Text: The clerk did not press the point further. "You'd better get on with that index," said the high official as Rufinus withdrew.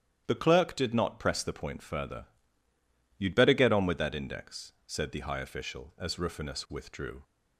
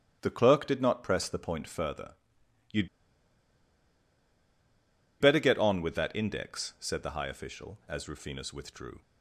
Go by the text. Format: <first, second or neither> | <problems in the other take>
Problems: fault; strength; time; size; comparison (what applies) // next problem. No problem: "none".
first | starts louder than the rest; strong; until 1.2 s; 11.5 dB; strong in the first // pauses between "You'd" and "better"; strong; at 2.8 s; 2.3 s long